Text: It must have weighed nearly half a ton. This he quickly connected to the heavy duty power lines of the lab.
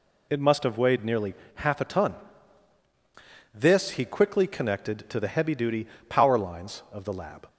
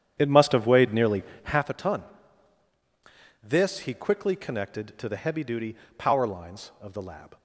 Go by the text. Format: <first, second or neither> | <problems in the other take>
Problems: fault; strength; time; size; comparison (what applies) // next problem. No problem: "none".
first | starts louder than the rest; strong; until 1.7 s; 9.5 dB // pauses between "nearly" and "half"; slight; at 1.2 s; 0.22 s long; slight in the first // pauses between "duty" and "power"; slight; at 5.7 s; 0.20 s long; slight in the first